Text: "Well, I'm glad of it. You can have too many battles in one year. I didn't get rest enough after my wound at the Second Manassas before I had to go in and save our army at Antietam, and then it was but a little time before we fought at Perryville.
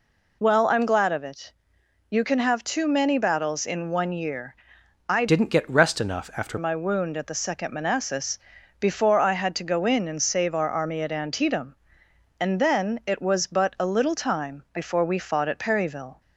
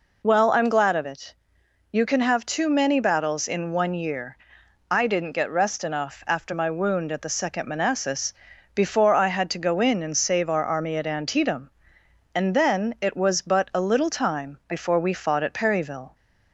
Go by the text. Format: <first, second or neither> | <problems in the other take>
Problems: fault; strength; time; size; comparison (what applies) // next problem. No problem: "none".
second | changes voice from "didn't" to "after"; from 5.2 to 6.5 s; 1.3 s long // pauses between "Manassas" and "before"; at 8.3 s; 0.42 s long; also in the second